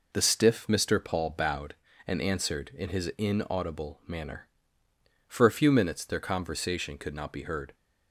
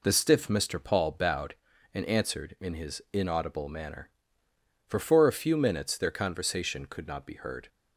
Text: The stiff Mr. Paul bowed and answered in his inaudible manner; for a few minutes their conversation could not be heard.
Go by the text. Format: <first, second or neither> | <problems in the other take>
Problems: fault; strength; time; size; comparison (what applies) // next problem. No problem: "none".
first | says "for" twice; at 5.0 s